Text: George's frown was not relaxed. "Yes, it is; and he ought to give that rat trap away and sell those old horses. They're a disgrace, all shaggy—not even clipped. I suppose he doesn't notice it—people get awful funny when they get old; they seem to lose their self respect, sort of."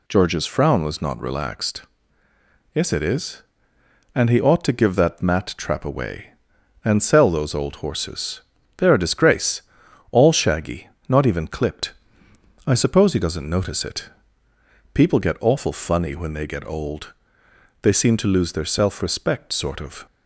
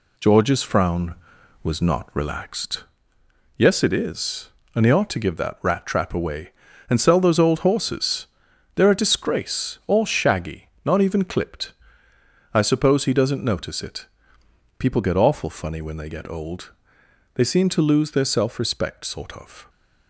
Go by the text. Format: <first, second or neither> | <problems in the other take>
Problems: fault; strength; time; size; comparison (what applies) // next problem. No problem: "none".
second | says "mat" for "rat"; at 5.2 s